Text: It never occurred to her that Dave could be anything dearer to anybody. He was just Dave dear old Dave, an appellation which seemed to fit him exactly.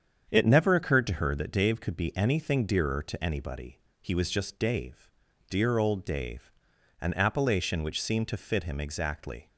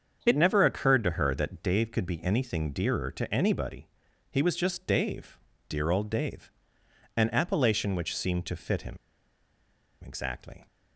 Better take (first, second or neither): first